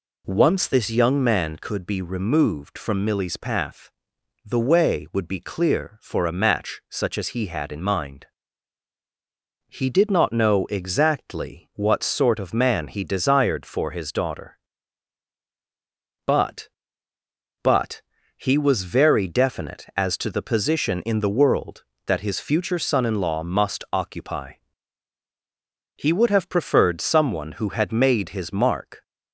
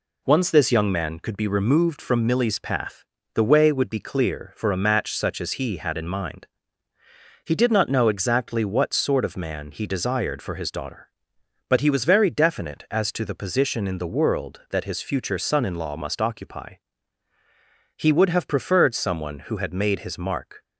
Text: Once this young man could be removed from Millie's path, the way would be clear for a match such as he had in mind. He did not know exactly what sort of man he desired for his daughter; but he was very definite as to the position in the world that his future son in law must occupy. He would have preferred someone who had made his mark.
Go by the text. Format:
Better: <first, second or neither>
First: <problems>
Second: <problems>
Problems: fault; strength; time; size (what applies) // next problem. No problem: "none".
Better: second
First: says "but" twice; at 17.6 s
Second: none